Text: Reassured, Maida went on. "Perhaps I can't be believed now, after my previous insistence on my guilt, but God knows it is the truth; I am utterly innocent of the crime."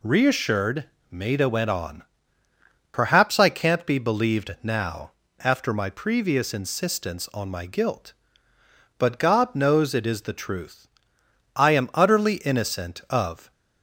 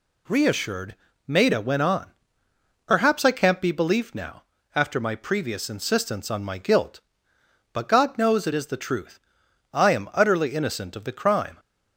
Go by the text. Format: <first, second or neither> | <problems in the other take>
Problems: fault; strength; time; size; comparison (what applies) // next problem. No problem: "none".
second | stops before "the crime"; at 13.5 s